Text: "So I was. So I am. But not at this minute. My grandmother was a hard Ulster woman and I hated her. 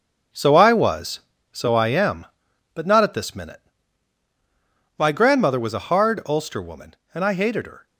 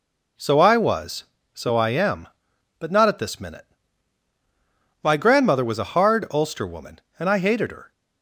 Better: second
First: gets quieter; strong; throughout; 9 dB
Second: none

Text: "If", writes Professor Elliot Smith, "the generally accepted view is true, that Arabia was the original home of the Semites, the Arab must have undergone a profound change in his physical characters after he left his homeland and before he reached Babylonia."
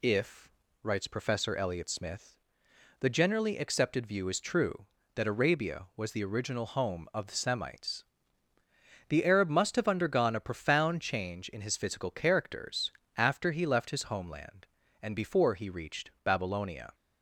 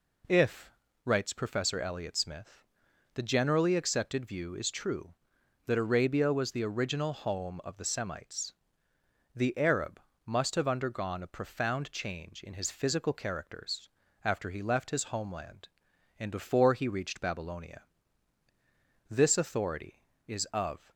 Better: first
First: pauses between "characters" and "after"; slight; at 12.9 s; 0.24 s long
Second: pauses between "Arab" and "must"; slight; at 10.0 s; 0.24 s long // pauses between "characters" and "after"; slight; at 13.8 s; 0.36 s long // goes on to say "This authority is of"; strong; from 19.1 s on; 1.8 s long

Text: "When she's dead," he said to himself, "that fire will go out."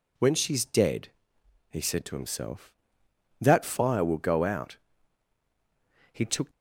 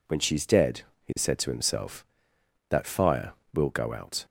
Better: second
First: goes on to say "He took"; slight; from 6.1 s on; 0.40 s long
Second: none

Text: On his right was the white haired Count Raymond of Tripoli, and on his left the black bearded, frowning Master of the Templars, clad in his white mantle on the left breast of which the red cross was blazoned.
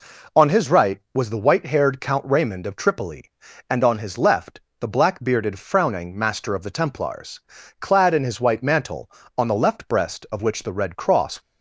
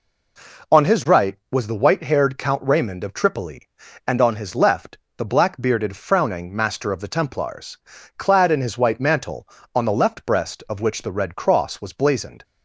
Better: second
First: pauses between "left" and "the"; slight; at 4.5 s; 0.18 s long // stops before "was blazoned"; at 11.4 s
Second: pauses between "left" and "the"; slight; at 4.9 s; 0.18 s long

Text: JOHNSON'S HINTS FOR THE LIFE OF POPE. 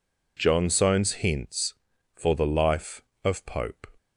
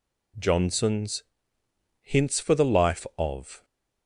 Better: first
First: none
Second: pauses between "JOHNSON'S" and "HINTS"; noticeable; at 1.2 s; 0.78 s long // stops before "POPE"; at 3.6 s

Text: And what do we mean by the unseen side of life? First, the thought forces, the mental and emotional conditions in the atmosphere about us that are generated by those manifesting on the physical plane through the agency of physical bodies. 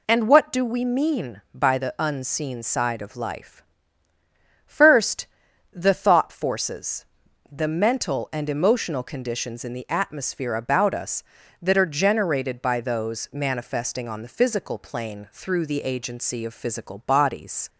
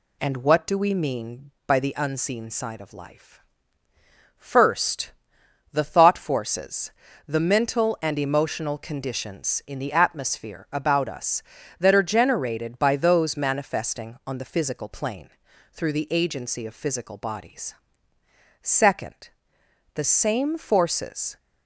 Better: first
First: none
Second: pauses between "plane" and "through"; at 15.2 s; 0.42 s long // goes on to say "Second the same forces"; strong; from 18.6 s on; 2.7 s long

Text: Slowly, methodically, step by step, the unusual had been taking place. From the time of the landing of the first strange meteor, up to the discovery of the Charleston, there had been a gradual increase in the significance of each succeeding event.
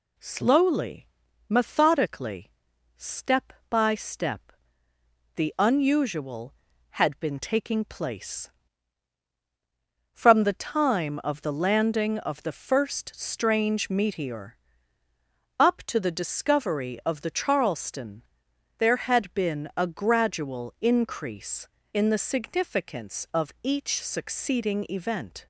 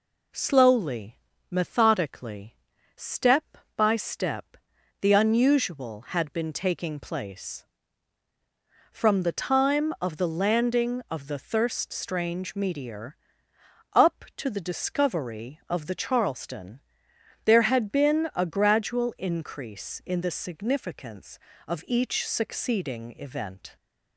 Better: first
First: none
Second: says "thirst" for "first"; at 11.3 s

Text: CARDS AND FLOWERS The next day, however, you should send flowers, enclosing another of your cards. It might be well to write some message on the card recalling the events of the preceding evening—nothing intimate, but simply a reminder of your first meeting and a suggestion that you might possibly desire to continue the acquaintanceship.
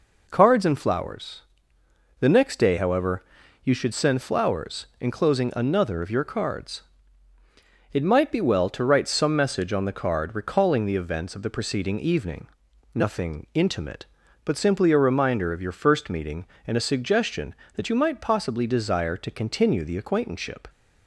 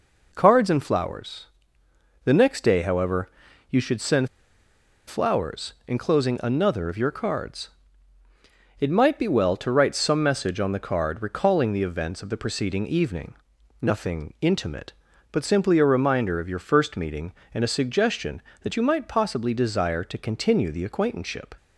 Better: first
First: pauses between "FLOWERS" and "The"; noticeable; at 1.4 s; 0.76 s long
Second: pauses between "FLOWERS" and "The"; noticeable; at 1.4 s; 0.76 s long // pauses between "send" and "flowers"; noticeable; at 4.2 s; 0.81 s long

